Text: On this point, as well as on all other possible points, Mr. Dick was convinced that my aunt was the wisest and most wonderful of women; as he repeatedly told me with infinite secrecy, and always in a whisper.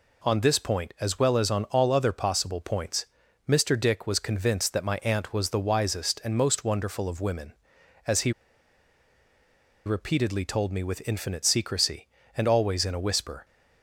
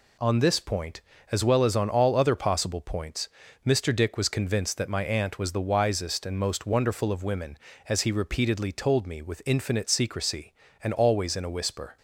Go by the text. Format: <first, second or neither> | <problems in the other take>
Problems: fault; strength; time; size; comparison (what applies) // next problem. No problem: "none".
second | pauses between "he" and "repeatedly"; strong; at 8.3 s; 1.5 s long